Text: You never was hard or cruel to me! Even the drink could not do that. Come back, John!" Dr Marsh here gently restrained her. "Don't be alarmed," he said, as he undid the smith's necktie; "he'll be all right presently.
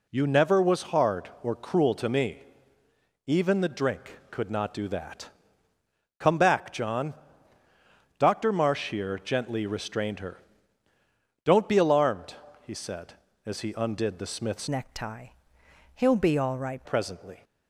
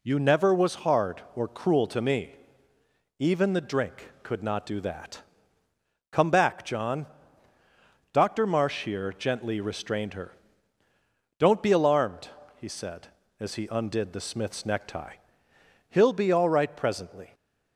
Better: second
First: changes voice from "necktie" to "right"; from 14.6 to 16.8 s; 2.2 s long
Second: none

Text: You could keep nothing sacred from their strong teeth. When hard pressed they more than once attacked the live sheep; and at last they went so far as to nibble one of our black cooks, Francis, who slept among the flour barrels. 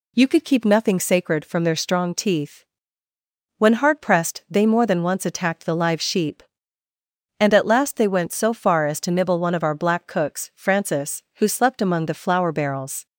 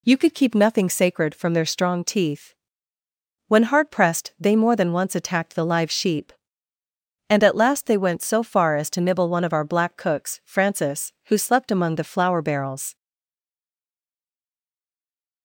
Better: first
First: none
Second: stays silent after the last word; from 12.9 s on; 2.5 s long

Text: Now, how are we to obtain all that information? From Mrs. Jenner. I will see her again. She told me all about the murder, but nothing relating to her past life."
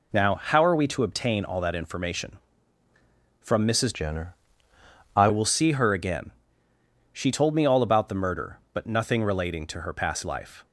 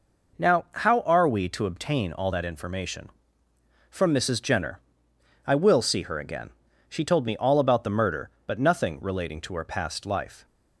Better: second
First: changes voice from "Jenner" to "I"; from 3.9 to 5.2 s; 1.3 s long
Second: none

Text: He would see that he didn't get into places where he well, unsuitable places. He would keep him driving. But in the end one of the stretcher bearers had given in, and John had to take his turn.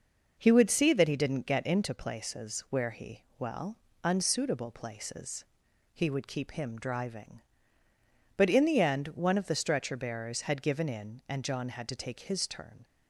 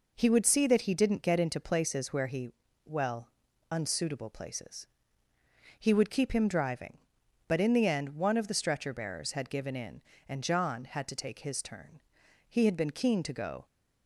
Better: first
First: pauses between "he" and "well"; slight; at 3.2 s; 0.16 s long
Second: pauses between "he" and "well"; slight; at 2.5 s; 0.34 s long // goes on to say "He had been keen to go"; noticeable; from 12.4 s on; 1.1 s long

